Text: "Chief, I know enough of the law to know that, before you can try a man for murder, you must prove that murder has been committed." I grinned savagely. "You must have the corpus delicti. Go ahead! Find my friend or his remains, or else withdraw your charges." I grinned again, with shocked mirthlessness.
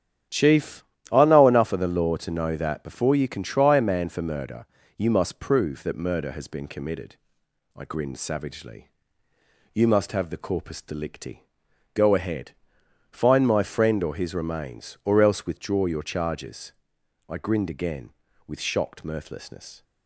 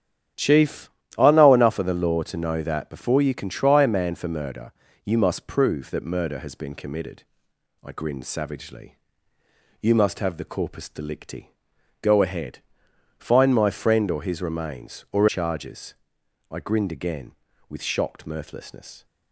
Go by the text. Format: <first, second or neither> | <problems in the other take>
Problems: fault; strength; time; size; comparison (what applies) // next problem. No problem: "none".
first | starts louder than the rest; strong; until 1.6 s; 9 dB; strong in the first // skips "else withdraw your"; at 15.2 s